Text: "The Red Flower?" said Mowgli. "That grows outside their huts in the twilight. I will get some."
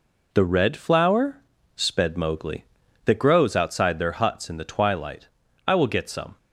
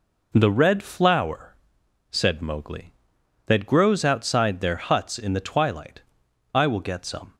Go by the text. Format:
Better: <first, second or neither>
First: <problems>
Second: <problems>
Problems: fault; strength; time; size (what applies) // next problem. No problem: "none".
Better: second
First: says "sped" for "said"; at 1.7 s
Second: none